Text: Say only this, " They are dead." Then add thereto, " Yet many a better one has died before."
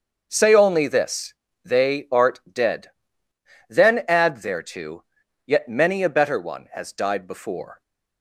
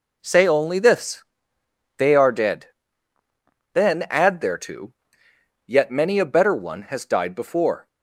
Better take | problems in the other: second | starts louder than the rest; until 1.3 s; 6.5 dB // says "art" for "are"; at 2.1 s

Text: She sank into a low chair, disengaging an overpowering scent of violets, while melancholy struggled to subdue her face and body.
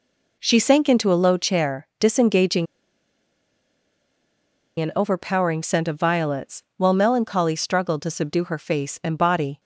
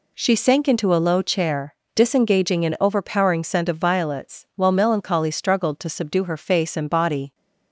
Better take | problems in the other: second | pauses between "disengaging" and "an"; strong; at 2.6 s; 2.1 s long

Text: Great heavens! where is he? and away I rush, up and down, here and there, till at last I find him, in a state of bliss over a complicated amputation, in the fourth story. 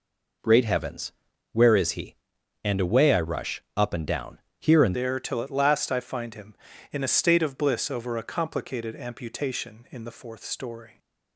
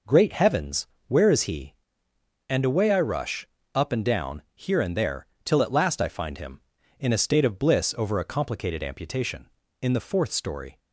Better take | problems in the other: second | changes voice at "there"; from 4.9 s on; 6.0 s long

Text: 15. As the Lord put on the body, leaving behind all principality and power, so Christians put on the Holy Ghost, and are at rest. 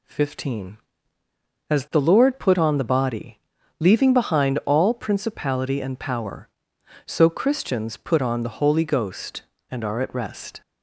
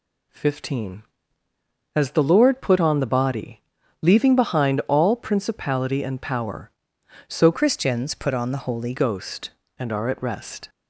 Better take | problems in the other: first | changes voice from "Christians" to "Holy"; from 7.5 to 8.9 s; 1.4 s long

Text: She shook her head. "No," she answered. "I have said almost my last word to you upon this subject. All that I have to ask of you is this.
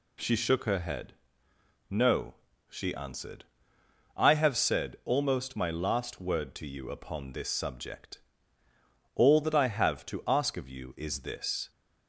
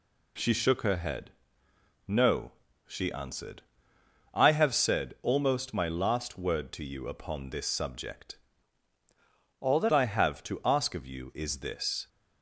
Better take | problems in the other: first | changes voice from "All" to "that"; from 9.5 to 9.9 s; 0.4 s long

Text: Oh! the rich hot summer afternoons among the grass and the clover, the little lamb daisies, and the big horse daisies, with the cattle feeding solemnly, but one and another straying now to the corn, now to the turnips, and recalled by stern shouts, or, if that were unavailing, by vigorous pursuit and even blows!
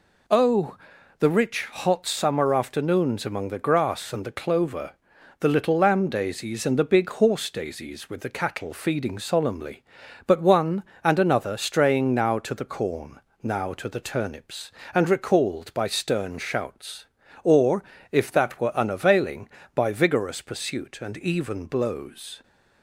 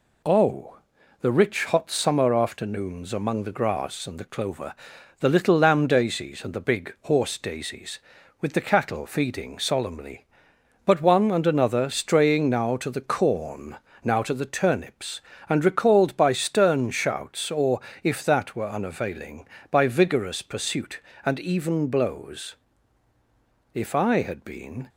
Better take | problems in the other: first | goes on to say "If I had been"; noticeable; from 23.7 s on; 1.1 s long

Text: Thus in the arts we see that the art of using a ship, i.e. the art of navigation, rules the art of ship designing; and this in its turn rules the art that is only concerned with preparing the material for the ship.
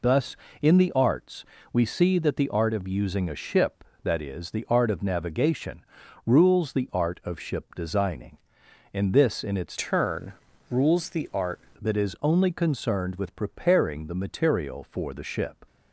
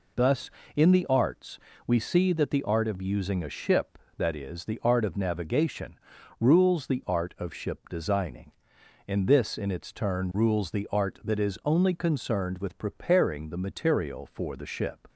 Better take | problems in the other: second | pauses between "arts" and "we"; slight; at 1.4 s; 0.28 s long; slight in the second // changes voice from "turn" to "art"; from 9.7 to 11.6 s; 1.9 s long // pauses between "turn" and "rules"; at 10.3 s; 0.38 s long

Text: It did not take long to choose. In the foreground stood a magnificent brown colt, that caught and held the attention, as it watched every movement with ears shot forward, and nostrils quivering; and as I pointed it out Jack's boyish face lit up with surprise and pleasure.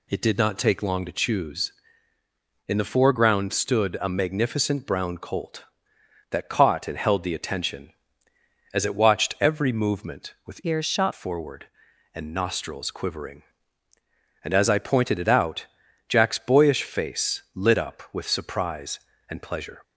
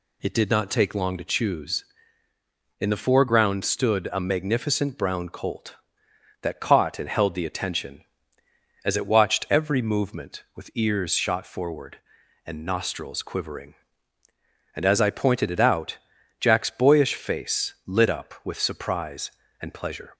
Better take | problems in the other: second | changes voice from "ears" to "shot"; from 10.6 to 11.1 s; 0.5 s long // pauses between "out" and "Jack's"; at 15.6 s; 0.42 s long; also in the second

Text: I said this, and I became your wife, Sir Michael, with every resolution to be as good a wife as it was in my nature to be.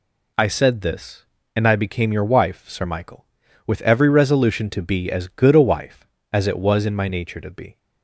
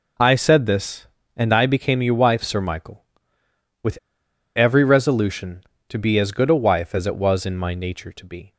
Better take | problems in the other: first | pauses between "with" and "every"; noticeable; at 3.9 s; 0.58 s long

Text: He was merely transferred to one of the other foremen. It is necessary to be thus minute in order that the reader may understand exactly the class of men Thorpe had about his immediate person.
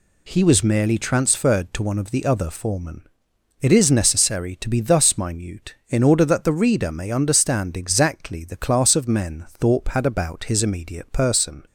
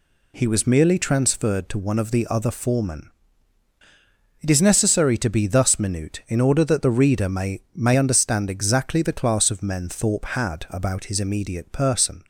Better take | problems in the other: first | says "may" twice; at 7.7 s

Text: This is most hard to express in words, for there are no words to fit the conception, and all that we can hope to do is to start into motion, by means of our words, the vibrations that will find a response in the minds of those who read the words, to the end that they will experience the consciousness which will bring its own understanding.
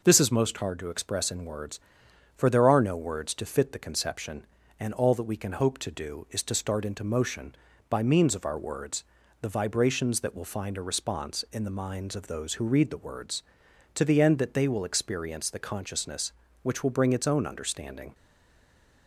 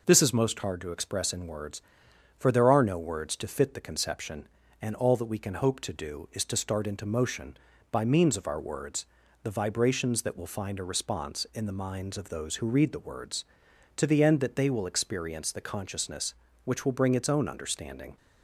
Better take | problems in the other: second | stays silent after the last word; slight; from 18.1 s on; 0.9 s long

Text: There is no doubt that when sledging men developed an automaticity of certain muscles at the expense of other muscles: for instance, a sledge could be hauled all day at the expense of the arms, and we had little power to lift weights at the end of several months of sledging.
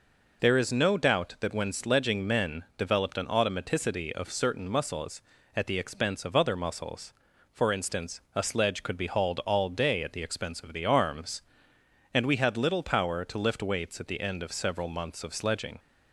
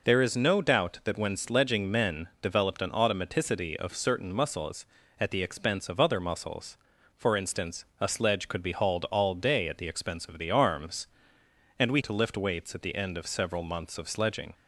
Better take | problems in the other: first | skips "had little power"; at 11.9 s

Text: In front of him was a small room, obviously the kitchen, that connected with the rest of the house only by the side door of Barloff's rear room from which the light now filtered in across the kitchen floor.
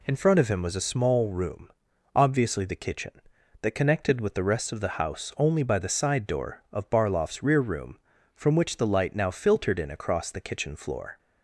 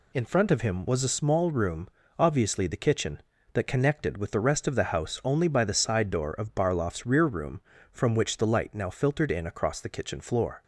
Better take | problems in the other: neither | none

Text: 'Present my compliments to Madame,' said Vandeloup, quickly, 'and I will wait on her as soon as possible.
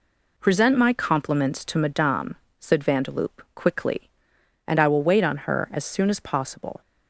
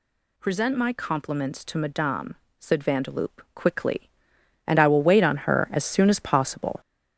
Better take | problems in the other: first | gets louder; noticeable; throughout; 5.5 dB

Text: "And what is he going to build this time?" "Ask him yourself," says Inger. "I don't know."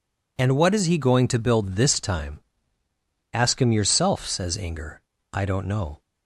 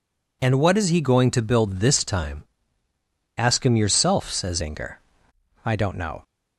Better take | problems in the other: first | changes voice at "Inger"; from 4.6 s on; 1.6 s long

